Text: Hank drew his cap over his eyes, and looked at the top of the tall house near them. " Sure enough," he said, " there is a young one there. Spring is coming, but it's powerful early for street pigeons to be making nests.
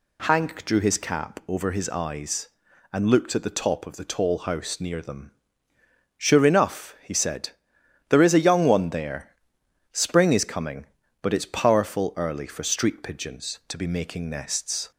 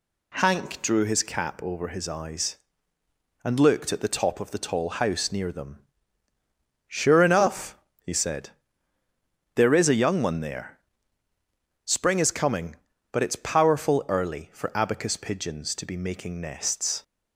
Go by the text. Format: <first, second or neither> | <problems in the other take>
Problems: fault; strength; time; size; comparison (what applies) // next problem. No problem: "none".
first | says "abacus" for "street"; at 14.7 s